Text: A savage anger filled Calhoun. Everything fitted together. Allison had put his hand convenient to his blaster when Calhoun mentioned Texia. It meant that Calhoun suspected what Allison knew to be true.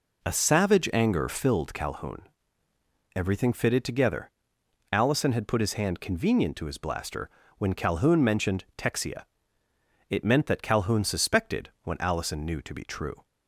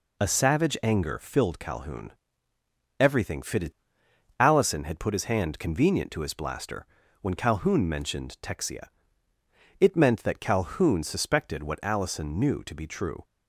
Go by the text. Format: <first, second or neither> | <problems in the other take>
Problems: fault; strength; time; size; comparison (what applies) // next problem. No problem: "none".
first | skips "together"; at 4.0 s // pauses between "blaster" and "when"; slight; at 6.8 s; 0.36 s long; slight in the first